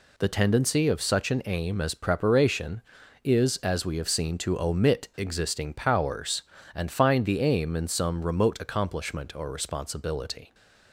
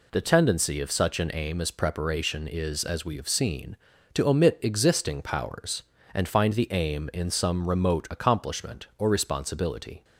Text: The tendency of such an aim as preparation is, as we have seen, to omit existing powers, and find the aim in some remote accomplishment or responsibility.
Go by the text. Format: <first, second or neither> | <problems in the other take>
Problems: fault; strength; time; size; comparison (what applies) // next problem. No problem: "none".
neither | none